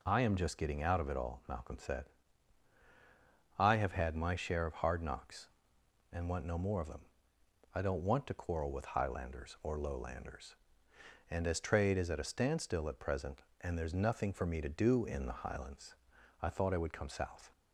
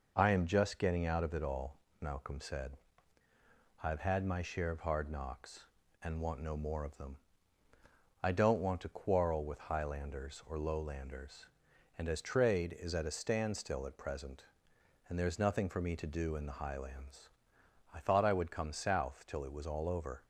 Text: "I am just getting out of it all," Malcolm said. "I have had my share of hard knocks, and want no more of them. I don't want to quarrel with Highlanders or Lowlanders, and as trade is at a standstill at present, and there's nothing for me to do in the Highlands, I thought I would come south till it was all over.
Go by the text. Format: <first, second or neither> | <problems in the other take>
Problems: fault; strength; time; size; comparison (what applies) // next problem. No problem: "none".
second | stops before "till it was all over"; at 17.5 s